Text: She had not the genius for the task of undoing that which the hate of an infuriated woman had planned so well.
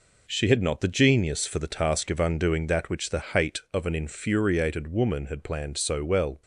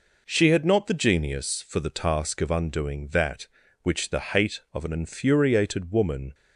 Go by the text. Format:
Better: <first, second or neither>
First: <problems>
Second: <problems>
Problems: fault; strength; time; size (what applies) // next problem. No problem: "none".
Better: first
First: none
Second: stops before "had planned so well"; at 6.3 s